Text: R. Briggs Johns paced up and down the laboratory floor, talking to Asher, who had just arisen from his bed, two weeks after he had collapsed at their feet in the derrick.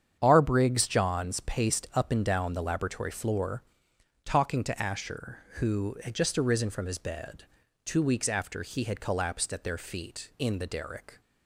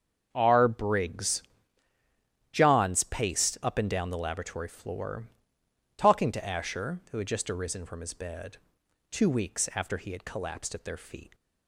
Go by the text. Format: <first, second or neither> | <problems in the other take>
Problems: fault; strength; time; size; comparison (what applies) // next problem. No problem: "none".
first | starts louder than the rest; until 1.3 s; 7 dB; strong in the first // pauses between "Briggs" and "Johns"; at 1.4 s; 1.1 s long // stops before "in the derrick"; at 11.3 s